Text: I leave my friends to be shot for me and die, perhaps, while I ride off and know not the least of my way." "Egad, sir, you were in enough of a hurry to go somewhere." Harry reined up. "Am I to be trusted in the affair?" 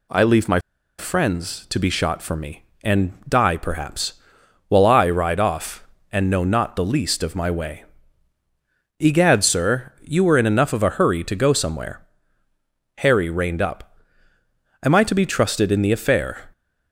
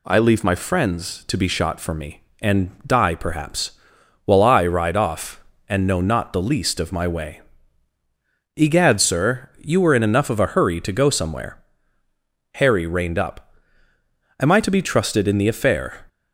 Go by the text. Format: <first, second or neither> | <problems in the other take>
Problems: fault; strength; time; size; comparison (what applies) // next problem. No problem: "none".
second | pauses between "my" and "friends"; at 0.5 s; 0.40 s long